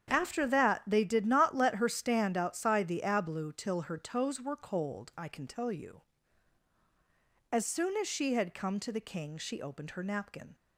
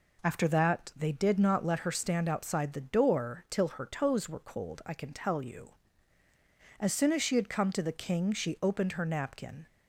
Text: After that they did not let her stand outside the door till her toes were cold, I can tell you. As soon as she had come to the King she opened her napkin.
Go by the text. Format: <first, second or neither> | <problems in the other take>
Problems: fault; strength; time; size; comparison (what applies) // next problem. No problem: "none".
second | starts louder than the rest; strong; until 1.1 s; 8.5 dB // says "ablu" for "door"; at 3.0 s